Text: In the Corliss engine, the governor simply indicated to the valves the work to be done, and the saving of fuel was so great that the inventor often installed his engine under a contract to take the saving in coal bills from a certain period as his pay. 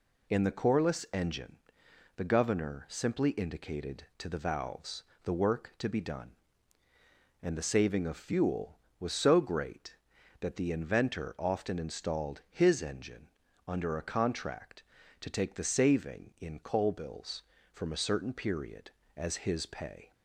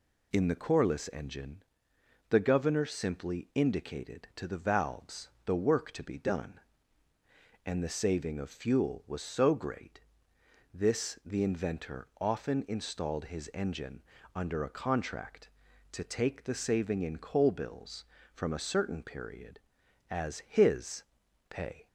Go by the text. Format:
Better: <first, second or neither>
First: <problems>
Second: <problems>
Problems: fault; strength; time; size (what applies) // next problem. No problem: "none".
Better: first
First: pauses between "valves" and "the"; slight; at 5.0 s; 0.22 s long // pauses between "engine" and "under"; at 13.2 s; 0.38 s long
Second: pauses between "valves" and "the"; slight; at 5.2 s; 0.16 s long // says "this" for "that"; at 10.7 s // pauses between "engine" and "under"; slight; at 14.0 s; 0.30 s long // pauses between "his" and "pay"; noticeable; at 21.0 s; 0.46 s long